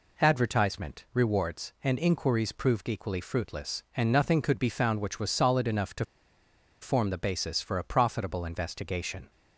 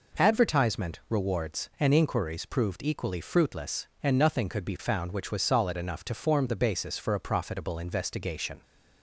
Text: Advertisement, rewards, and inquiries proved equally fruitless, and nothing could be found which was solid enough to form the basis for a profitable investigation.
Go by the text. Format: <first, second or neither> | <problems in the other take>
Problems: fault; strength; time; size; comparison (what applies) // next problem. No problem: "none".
second | pauses between "to" and "form"; noticeable; at 6.0 s; 0.77 s long